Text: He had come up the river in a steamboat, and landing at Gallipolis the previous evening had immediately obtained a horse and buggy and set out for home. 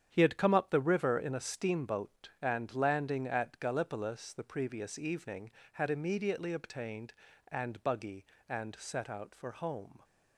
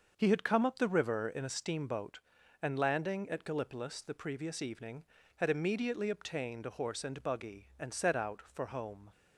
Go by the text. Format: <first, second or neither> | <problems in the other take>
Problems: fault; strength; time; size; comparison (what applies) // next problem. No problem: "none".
second | starts louder than the rest; strong; until 1.1 s; 8.5 dB; also in the second // skips "a horse"; at 7.2 s